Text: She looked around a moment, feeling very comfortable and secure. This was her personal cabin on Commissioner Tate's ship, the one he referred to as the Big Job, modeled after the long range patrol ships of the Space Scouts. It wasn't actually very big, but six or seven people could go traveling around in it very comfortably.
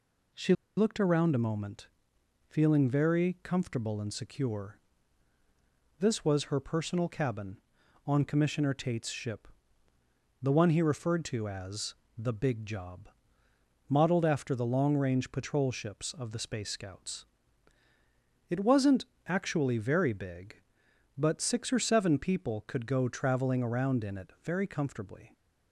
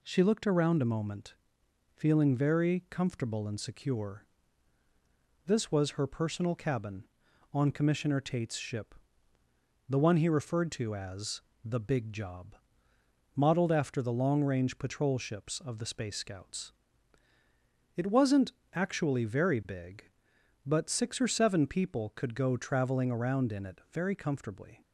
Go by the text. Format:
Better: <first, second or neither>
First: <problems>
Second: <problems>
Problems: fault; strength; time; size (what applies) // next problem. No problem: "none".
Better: second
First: pauses between "She" and "looked"; slight; at 0.5 s; 0.22 s long // pauses between "as" and "the"; slight; at 11.9 s; 0.24 s long // pauses between "wasn't" and "actually"; slight; at 19.0 s; 0.22 s long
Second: pauses between "as" and "the"; slight; at 11.4 s; 0.24 s long // pauses between "wasn't" and "actually"; slight; at 18.5 s; 0.22 s long